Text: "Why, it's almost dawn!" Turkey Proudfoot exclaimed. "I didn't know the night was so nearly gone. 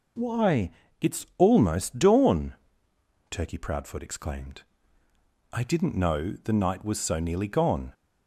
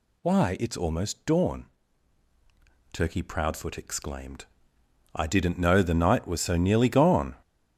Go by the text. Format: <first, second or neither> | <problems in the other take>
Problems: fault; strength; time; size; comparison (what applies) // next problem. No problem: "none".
neither | none